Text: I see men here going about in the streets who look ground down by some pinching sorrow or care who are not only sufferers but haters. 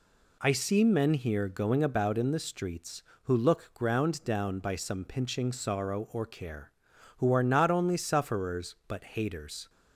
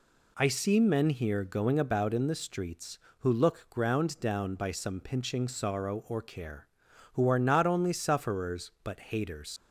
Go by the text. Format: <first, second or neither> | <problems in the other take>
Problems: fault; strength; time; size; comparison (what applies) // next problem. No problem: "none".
first | leaves "haters" unfinished; at 9.5 s; 90 ms